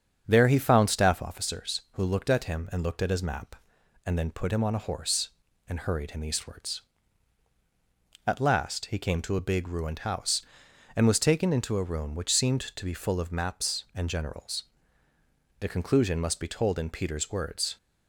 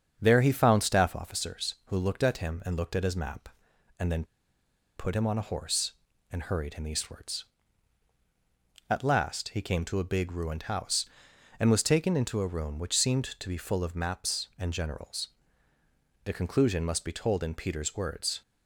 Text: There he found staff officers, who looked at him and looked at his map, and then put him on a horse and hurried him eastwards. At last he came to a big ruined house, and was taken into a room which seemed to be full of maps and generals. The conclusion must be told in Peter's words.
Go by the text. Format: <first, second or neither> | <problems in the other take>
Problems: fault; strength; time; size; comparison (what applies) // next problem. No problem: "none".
first | starts louder than the rest; strong; until 1.2 s; 7 dB; strong in the first // pauses between "then" and "put"; noticeable; at 4.2 s; 0.72 s long